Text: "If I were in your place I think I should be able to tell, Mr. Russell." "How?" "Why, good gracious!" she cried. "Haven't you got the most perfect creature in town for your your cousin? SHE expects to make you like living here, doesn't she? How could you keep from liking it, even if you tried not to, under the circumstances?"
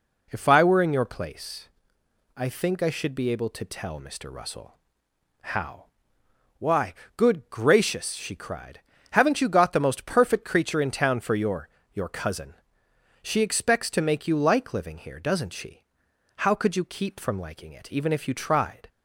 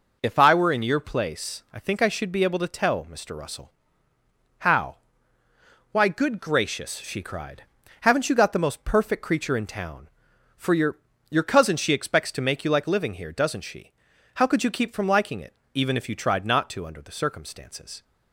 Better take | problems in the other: second | pauses between "place" and "I"; noticeable; at 1.6 s; 0.70 s long // pauses between "your" and "your"; slight; at 11.6 s; 0.24 s long; slight in the second // stops before "not to under the circumstances"; at 18.8 s

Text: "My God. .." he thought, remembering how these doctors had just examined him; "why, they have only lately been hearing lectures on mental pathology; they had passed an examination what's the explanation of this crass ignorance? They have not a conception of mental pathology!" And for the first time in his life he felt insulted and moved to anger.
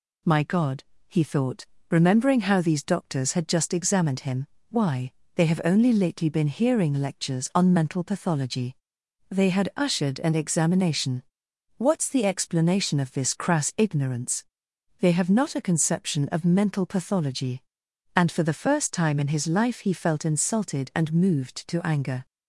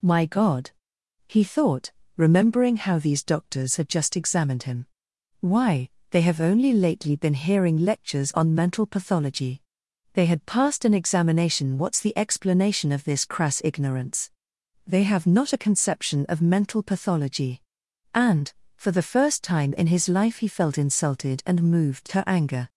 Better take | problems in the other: second | says "ushered" for "passed"; at 9.7 s // pauses between "examination" and "what's"; noticeable; at 11.2 s; 0.56 s long

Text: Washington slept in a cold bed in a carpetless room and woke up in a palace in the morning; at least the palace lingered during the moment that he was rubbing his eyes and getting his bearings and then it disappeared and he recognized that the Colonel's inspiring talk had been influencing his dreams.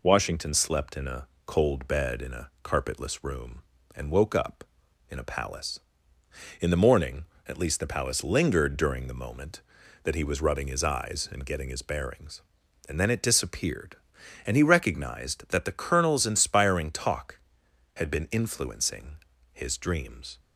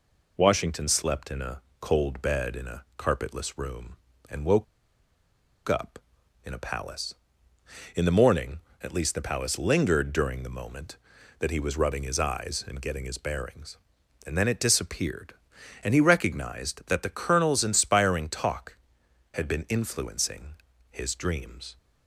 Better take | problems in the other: first | pauses between "a" and "cold"; slight; at 1.6 s; 0.20 s long; slight in the first // pauses between "woke" and "up"; at 4.6 s; 1.0 s long // pauses between "influencing" and "his"; at 20.5 s; 0.38 s long; also in the first

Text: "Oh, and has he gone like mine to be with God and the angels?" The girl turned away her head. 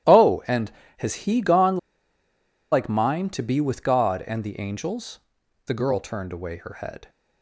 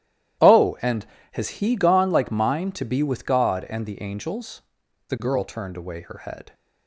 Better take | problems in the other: second | starts louder than the rest; strong; until 1.4 s; 13 dB; strong in the second // pauses between "gone" and "like"; noticeable; at 1.7 s; 0.94 s long

